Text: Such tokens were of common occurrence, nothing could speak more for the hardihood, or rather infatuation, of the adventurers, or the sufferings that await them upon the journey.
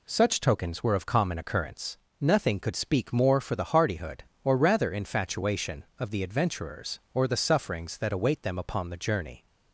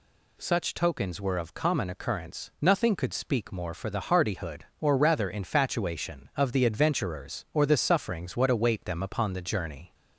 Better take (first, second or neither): first